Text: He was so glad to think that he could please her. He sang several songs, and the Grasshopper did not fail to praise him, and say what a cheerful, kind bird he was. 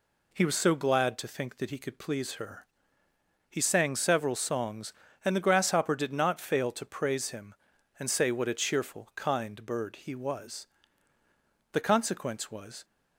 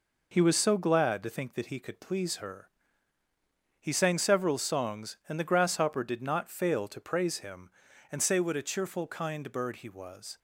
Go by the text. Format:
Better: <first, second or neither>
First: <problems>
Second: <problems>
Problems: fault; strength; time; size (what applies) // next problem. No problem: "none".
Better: second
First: goes on to say "The consequence was"; noticeable; from 11.7 s on; 1.1 s long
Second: none